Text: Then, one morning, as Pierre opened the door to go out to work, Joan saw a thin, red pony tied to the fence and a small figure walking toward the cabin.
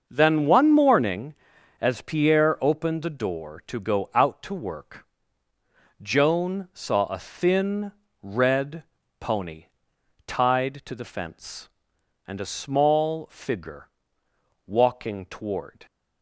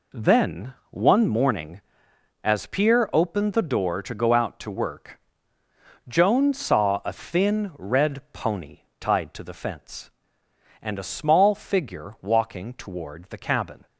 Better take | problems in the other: second | starts louder than the rest; until 1.1 s; 6.5 dB // pauses between "red" and "pony"; slight; at 8.8 s; 0.36 s long // pauses between "pony" and "tied"; noticeable; at 9.6 s; 0.62 s long; slight in the second // pauses between "figure" and "walking"; noticeable; at 13.8 s; 0.80 s long // stops before "the cabin"; at 15.8 s

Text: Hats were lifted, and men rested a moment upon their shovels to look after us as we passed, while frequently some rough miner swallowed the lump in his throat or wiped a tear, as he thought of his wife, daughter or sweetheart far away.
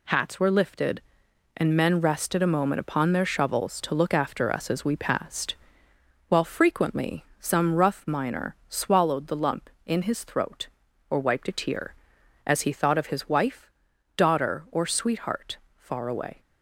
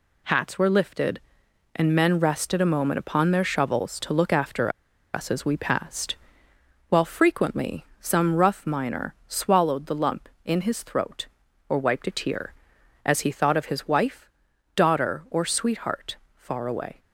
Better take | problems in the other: first | pauses between "after" and "us"; at 4.7 s; 0.42 s long // pauses between "frequently" and "some"; slight; at 7.8 s; 0.16 s long; slight in the first // pauses between "sweetheart" and "far"; slight; at 16.1 s; 0.18 s long; slight in the first

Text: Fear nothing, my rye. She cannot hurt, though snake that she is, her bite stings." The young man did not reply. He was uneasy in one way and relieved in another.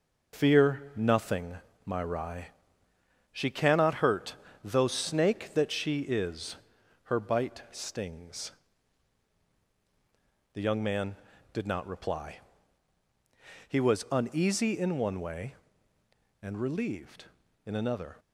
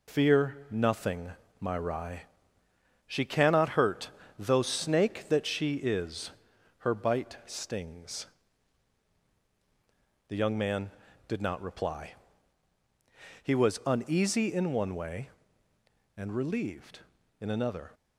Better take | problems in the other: second | starts louder than the rest; noticeable; until 1.4 s; 5.5 dB

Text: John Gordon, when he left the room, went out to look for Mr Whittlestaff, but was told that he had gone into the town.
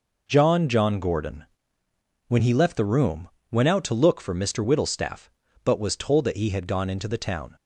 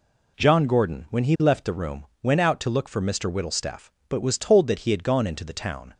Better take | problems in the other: second | says "John" twice; at 0.6 s

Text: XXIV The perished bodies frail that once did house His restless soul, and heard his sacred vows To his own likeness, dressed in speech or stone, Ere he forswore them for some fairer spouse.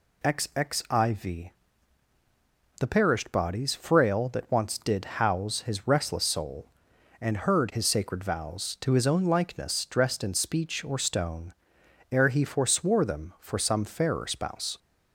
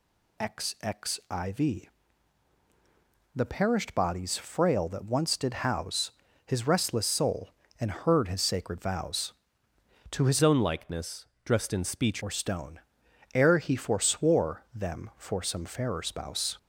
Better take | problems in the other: first | pauses between "XXIV" and "The"; strong; at 1.8 s; 1.4 s long; strong in the first // pauses between "house" and "His"; slight; at 6.1 s; 0.34 s long // changes voice from "own" to "speech"; from 10.4 to 12.2 s; 1.8 s long

